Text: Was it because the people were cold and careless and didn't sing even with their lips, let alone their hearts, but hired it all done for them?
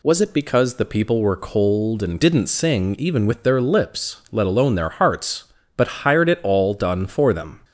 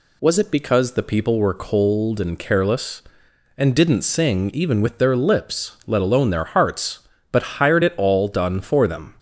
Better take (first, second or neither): second